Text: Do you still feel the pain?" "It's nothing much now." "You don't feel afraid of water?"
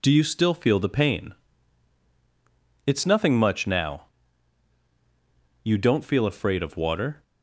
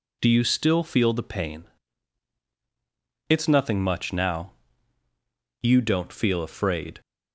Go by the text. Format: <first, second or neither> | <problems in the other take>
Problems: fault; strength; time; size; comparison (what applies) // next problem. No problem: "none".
first | stops before "of water"; at 7.0 s